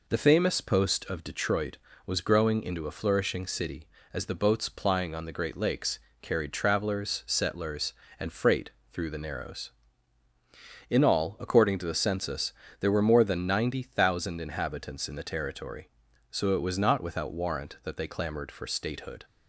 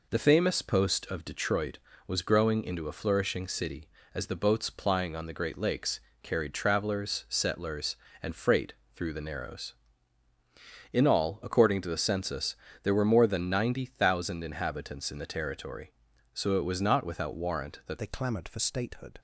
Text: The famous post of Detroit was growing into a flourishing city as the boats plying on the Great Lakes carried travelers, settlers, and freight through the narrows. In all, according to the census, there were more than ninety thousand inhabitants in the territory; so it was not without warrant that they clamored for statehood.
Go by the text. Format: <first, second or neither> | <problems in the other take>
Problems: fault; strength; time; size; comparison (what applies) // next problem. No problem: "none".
first | pauses between "Lakes" and "carried"; slight; at 5.9 s; 0.24 s long; slight in the first // pauses between "freight" and "through"; slight; at 8.7 s; 0.20 s long; slight in the first // changes voice at "they"; from 17.9 s on; 1.2 s long